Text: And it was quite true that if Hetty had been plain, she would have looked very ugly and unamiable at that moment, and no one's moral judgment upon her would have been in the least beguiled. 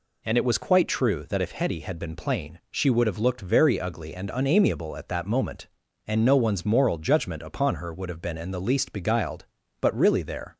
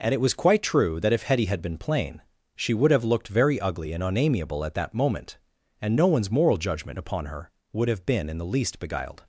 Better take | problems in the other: second | goes on to say "But really there"; noticeable; from 9.8 s on; 0.74 s long

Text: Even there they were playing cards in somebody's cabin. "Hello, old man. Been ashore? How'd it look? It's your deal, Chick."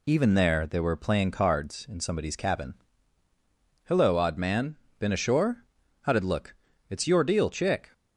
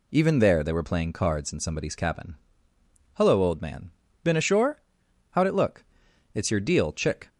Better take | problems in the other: second | says "odd" for "old"; at 4.1 s

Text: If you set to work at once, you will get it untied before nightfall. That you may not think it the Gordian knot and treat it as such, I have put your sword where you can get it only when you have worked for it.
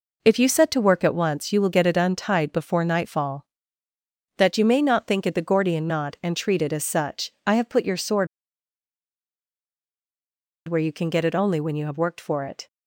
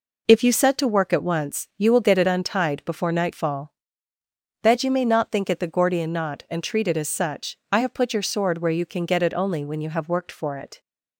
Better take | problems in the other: second | pauses between "sword" and "where"; strong; at 8.2 s; 2.3 s long

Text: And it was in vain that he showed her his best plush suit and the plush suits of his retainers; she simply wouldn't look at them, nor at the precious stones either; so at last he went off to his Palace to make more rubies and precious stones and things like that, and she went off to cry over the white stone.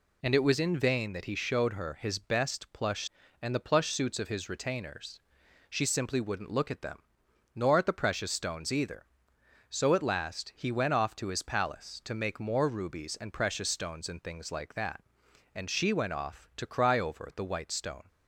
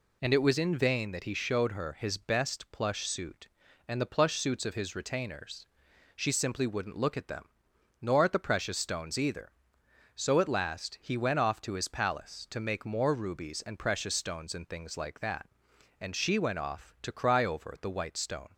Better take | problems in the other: second | skips "suit"; at 3.2 s

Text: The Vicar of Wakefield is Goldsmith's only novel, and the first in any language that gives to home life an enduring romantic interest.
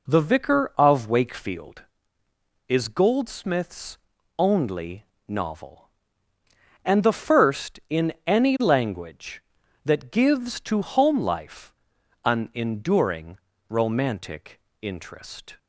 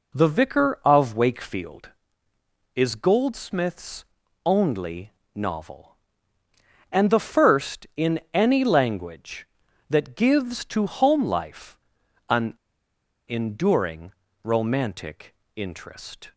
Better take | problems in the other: first | pauses between "Goldsmith's" and "only"; at 4.0 s; 0.40 s long; also in the first // pauses between "only" and "novel"; slight; at 5.1 s; 0.24 s long; slight in the first // pauses between "life" and "an"; noticeable; at 11.7 s; 0.50 s long; noticeable in the first // pauses between "an" and "enduring"; noticeable; at 12.5 s; 0.75 s long // pauses between "enduring" and "romantic"; slight; at 14.1 s; 0.32 s long; slight in the first // pauses between "romantic" and "interest"; slight; at 15.3 s; 0.18 s long; slight in the first

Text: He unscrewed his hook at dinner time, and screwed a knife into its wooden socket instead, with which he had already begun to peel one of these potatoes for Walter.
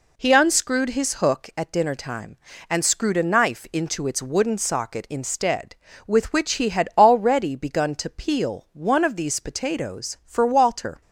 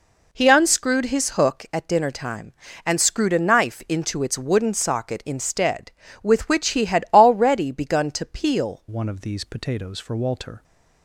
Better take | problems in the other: first | changes voice at "one"; from 8.8 s on; 1.8 s long

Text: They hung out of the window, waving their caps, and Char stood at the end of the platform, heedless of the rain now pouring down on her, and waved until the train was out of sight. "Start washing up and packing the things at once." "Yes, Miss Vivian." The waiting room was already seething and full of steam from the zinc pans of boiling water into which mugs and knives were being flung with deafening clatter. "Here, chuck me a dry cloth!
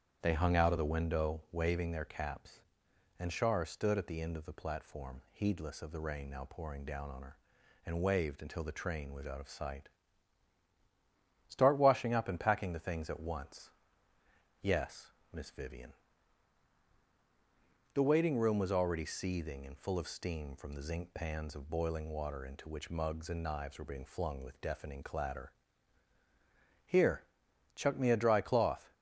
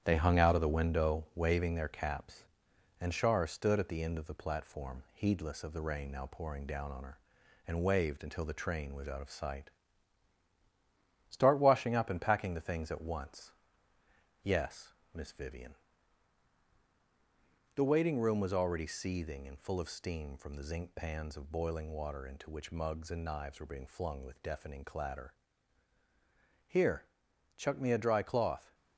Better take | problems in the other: first | gets quieter; noticeable; throughout; 5.5 dB // starts louder than the rest; strong; until 1.0 s; 9 dB; strong in the first

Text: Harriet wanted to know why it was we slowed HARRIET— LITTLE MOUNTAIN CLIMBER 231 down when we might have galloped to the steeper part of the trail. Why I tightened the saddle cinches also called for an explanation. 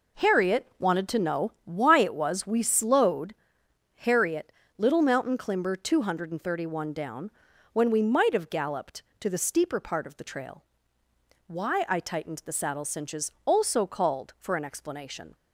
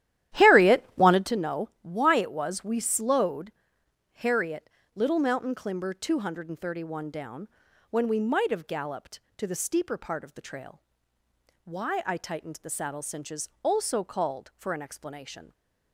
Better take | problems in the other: first | starts louder than the rest; strong; until 1.4 s; 12.5 dB // pauses between "slowed" and "HARRIET"; noticeable; at 3.5 s; 0.62 s long; noticeable in the first // pauses between "down" and "when"; at 7.4 s; 0.42 s long; also in the first

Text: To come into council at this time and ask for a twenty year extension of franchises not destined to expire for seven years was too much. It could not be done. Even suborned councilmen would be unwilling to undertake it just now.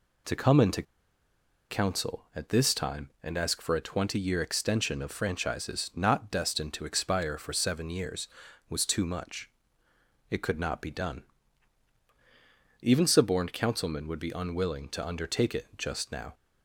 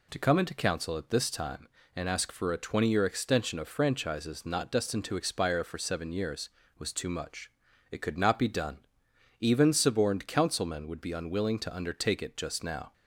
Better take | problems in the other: second | pauses between "into" and "council"; noticeable; at 0.8 s; 0.87 s long

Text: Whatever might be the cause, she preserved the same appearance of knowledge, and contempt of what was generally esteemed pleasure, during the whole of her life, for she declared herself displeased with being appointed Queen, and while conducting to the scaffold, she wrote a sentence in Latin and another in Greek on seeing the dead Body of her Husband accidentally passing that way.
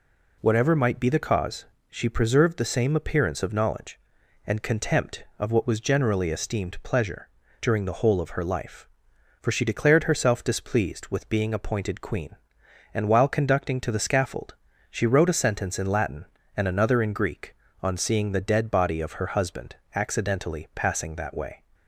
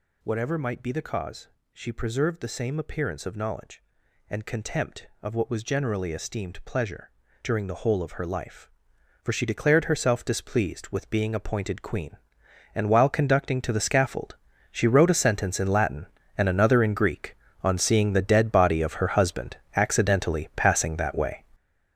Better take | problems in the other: first | gets louder; strong; throughout; 9.5 dB // pauses between "Husband" and "accidentally"; slight; at 19.5 s; 0.22 s long; slight in the first

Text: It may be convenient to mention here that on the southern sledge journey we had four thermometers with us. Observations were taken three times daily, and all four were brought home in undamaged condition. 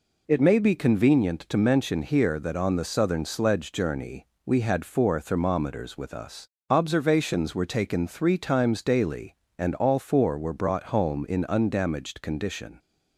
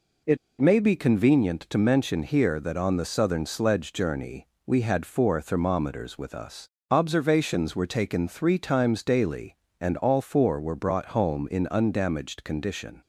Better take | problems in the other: first | pauses between "It" and "may"; slight; at 0.3 s; 0.23 s long // pauses between "journey" and "we"; slight; at 4.4 s; 0.20 s long; slight in the first

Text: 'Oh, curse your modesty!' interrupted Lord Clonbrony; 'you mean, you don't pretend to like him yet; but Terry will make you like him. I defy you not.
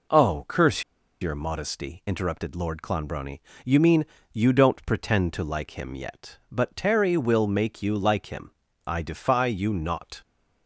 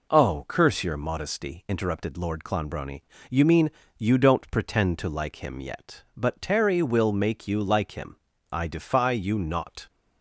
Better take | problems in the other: second | pauses between "curse" and "your"; at 0.8 s; 0.38 s long

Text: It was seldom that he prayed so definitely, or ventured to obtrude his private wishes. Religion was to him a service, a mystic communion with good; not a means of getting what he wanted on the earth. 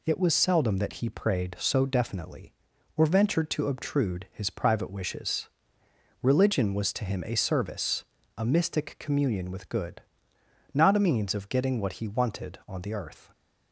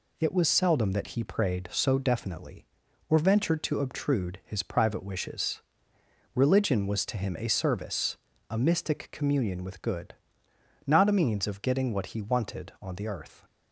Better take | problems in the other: neither | none

